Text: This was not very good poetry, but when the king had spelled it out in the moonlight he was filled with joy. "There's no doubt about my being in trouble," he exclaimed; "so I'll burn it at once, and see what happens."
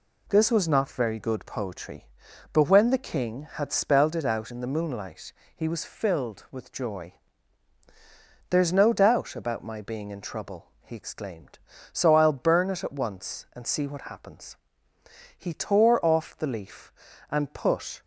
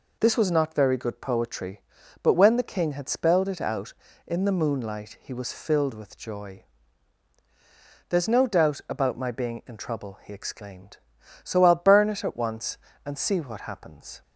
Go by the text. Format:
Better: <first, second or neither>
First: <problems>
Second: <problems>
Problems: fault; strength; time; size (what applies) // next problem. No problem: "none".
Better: second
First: pauses between "moonlight" and "he"; slight; at 5.3 s; 0.24 s long // goes on to say "He tore off the leaf and put"; strong; from 15.3 s on; 2.6 s long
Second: none